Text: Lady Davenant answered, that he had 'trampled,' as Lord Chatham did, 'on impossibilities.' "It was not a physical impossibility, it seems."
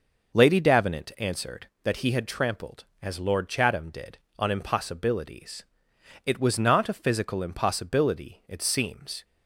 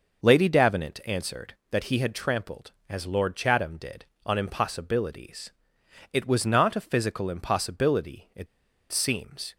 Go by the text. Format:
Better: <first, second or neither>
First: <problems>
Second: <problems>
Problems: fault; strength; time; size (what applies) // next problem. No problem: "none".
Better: first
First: none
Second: pauses between "it" and "seems"; at 8.4 s; 0.45 s long